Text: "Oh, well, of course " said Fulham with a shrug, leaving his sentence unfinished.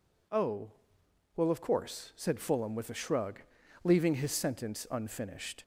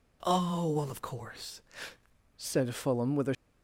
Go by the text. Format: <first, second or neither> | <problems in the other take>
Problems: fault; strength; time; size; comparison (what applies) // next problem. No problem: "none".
first | stops before "shrug leaving his sentence unfinished"; at 3.3 s